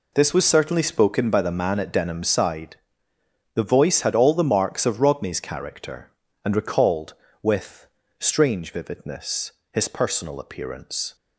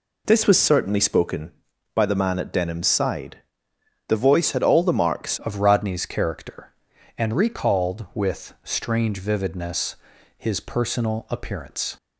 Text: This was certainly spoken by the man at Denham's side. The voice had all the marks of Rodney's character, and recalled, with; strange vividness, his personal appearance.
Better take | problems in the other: first | changes voice at "of"; from 5.3 s on; 6.6 s long

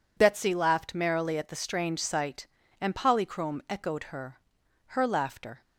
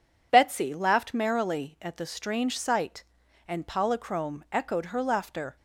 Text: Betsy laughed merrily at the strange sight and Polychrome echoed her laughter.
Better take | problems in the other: second | says "her" twice; at 4.8 s

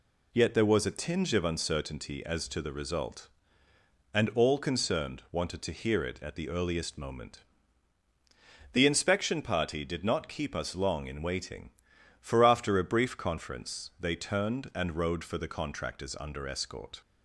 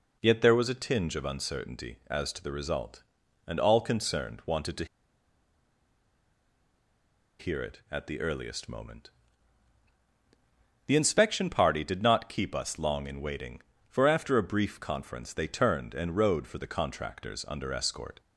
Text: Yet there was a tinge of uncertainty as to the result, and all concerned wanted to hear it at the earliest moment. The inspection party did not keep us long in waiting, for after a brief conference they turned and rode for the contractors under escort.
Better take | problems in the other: first | pauses between "to" and "hear"; strong; at 4.8 s; 2.5 s long

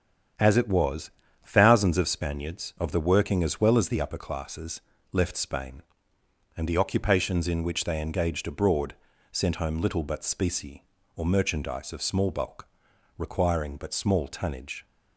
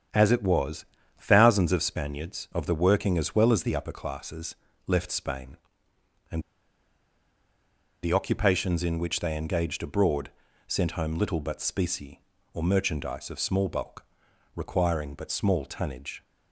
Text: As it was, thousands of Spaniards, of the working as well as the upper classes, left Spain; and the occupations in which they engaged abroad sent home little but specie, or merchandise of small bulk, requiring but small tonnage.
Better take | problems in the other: first | starts louder than the rest; strong; until 1.4 s; 8.5 dB; strong in the first // pauses between "and" and "the"; strong; at 6.4 s; 1.6 s long // pauses between "abroad" and "sent"; slight; at 10.3 s; 0.36 s long; slight in the first

